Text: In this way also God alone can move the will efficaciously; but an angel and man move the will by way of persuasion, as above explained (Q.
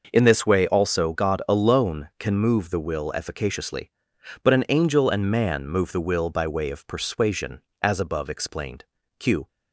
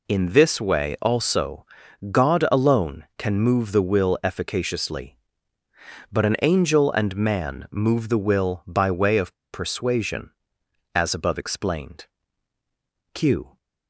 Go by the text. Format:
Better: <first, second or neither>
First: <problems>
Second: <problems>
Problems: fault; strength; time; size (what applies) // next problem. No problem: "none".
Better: first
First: none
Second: pauses between "also" and "God"; noticeable; at 1.6 s; 0.46 s long // pauses between "of" and "persuasion"; slight; at 9.3 s; 0.19 s long